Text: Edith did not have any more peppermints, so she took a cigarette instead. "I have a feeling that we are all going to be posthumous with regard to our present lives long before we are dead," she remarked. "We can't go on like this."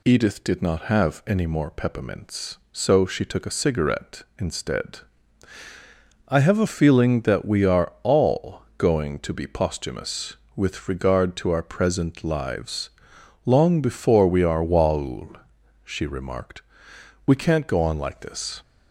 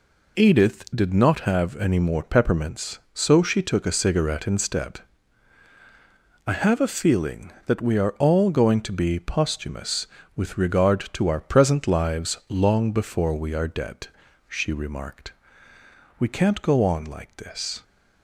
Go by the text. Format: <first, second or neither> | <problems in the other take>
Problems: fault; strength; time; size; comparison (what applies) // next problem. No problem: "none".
second | pauses between "all" and "going"; slight; at 8.6 s; 0.16 s long // pauses between "lives" and "long"; noticeable; at 12.8 s; 0.56 s long // says "waul" for "dead"; at 14.6 s